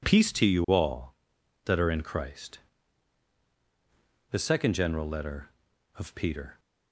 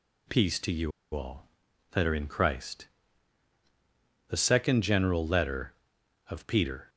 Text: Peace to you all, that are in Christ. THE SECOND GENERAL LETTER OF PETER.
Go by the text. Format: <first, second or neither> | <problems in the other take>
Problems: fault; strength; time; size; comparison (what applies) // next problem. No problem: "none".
first | pauses between "you" and "all"; slight; at 0.9 s; 0.23 s long